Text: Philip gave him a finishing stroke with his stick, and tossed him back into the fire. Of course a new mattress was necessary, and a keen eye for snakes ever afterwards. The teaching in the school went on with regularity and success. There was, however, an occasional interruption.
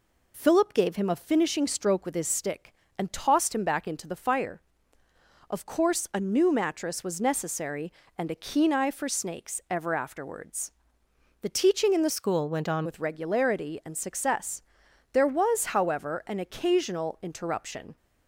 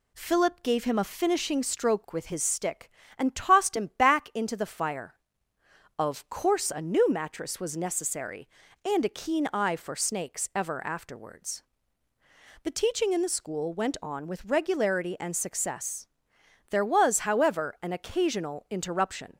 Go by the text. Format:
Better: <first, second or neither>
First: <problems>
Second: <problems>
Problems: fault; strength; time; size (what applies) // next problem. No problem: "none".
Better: second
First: changes voice from "school" to "on"; from 12.1 to 12.8 s; 0.7 s long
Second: none